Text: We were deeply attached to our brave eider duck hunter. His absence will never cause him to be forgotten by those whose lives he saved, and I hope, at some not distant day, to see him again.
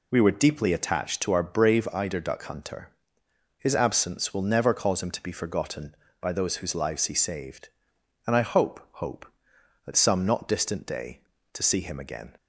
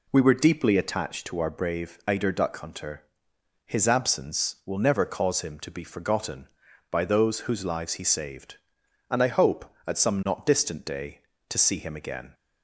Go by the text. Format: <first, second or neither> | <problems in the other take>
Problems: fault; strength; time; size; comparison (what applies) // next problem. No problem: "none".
second | says "hope" twice; at 8.9 s